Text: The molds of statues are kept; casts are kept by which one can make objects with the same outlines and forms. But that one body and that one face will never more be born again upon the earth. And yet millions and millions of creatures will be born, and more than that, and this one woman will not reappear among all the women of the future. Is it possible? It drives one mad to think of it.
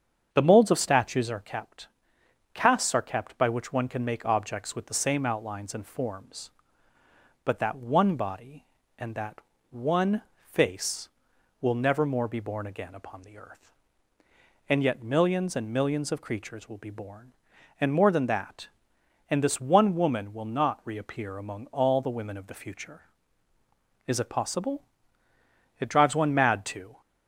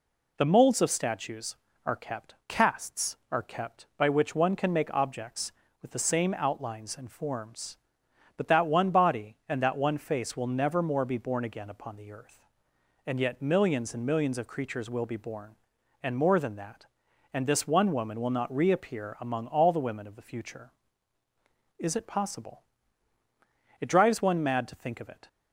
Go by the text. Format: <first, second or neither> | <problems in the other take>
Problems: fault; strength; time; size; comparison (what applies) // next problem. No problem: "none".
second | starts louder than the rest; strong; until 1.3 s; 7.5 dB // pauses between "that" and "one"; slight; at 9.3 s; 0.32 s long // pauses between "one" and "face"; slight; at 10.2 s; 0.28 s long // stops before "think of it"; at 27.0 s